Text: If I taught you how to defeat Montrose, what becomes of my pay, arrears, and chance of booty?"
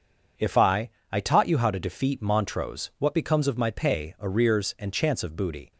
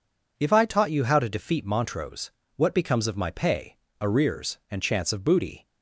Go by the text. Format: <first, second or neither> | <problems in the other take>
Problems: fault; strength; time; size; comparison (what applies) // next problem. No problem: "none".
second | says "I" twice; at 1.0 s